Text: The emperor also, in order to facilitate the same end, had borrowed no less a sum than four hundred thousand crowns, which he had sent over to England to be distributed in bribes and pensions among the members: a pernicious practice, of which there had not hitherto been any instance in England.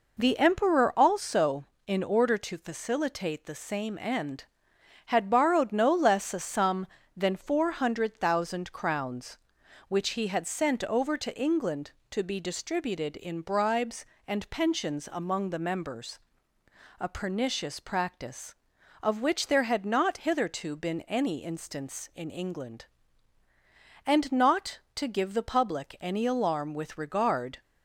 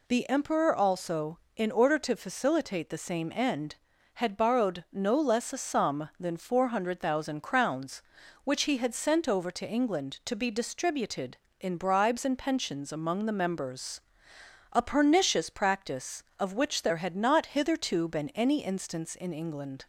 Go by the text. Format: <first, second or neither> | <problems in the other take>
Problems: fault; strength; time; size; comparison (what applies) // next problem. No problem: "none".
second | goes on to say "And not to give the public any alarm with regard"; strong; from 24.0 s on; 3.5 s long